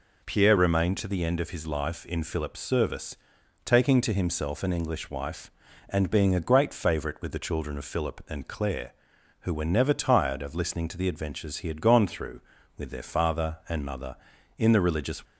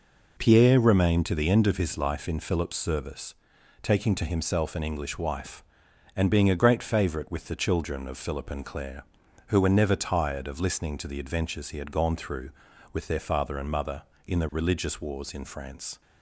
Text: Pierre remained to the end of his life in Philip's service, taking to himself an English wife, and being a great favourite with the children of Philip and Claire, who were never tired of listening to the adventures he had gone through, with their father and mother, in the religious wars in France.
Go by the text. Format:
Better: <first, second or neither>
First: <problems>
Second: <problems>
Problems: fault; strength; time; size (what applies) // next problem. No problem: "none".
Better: second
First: stops before "wars in France"; at 15.2 s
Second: none